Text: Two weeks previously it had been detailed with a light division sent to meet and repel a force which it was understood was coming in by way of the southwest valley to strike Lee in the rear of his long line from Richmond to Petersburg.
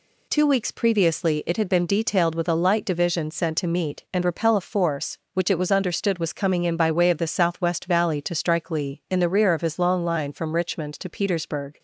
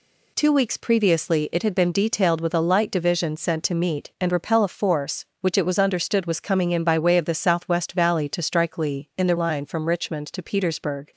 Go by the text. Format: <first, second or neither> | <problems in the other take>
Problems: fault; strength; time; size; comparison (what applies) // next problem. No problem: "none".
first | skips "rear of his long"; at 9.3 s